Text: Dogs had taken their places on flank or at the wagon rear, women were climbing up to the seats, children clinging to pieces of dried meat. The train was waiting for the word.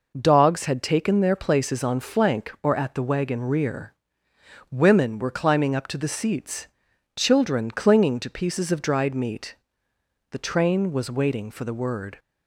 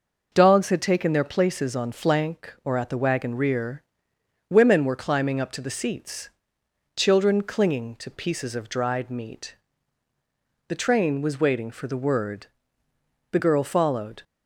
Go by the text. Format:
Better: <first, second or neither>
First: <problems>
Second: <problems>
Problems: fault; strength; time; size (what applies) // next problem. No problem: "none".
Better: first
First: none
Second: goes on to say "The girl followed"; noticeable; from 13.3 s on; 0.90 s long